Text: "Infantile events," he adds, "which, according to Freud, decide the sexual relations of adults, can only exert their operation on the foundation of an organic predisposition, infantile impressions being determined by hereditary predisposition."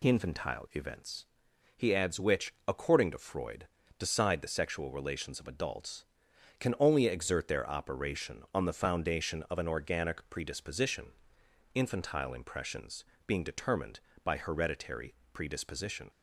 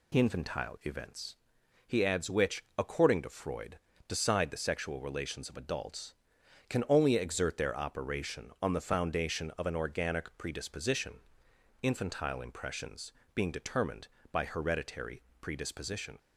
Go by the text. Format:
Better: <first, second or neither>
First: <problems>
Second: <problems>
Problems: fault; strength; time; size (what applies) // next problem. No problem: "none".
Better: neither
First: pauses between "impressions" and "being"; slight; at 13.0 s; 0.24 s long // pauses between "hereditary" and "predisposition"; slight; at 15.1 s; 0.20 s long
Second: pauses between "impressions" and "being"; slight; at 13.1 s; 0.24 s long // pauses between "hereditary" and "predisposition"; slight; at 15.2 s; 0.20 s long